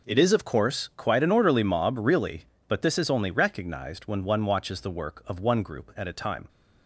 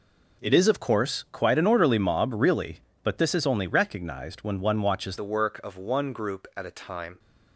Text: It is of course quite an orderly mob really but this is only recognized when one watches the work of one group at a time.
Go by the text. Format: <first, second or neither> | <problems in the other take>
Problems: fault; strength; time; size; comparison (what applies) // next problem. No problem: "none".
first | changes voice at "the"; from 5.1 s on; 2.0 s long